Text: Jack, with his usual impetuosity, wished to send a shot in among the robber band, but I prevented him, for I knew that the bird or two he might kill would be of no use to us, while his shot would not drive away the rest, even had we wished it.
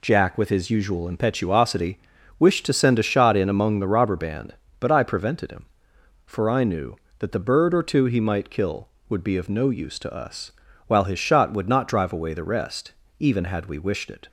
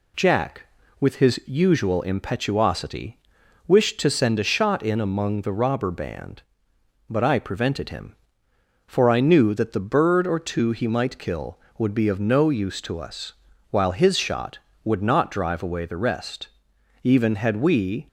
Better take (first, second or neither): first